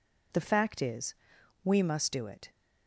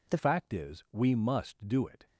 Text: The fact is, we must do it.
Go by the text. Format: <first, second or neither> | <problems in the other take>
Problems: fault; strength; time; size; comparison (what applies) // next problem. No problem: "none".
first | changes voice at "fact"; from 0.1 s on; 1.9 s long